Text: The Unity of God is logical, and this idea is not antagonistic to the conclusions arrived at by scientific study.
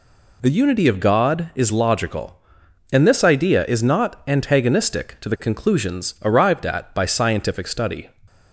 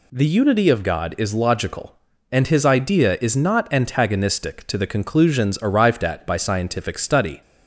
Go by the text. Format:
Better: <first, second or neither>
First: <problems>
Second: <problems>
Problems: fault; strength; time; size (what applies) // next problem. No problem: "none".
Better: first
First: none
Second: says "his" for "this"; at 2.4 s